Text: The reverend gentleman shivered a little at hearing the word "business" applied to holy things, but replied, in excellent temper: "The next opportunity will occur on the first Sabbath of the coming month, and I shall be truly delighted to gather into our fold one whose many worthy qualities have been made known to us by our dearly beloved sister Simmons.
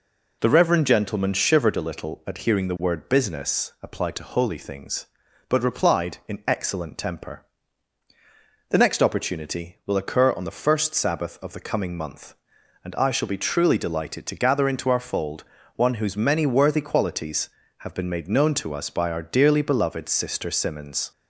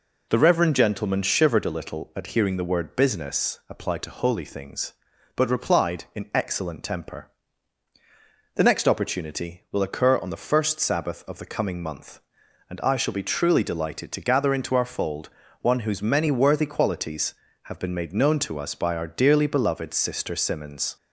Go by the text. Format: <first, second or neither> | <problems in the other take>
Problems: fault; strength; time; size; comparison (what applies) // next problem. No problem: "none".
neither | pauses between "fold" and "one"; slight; the same in both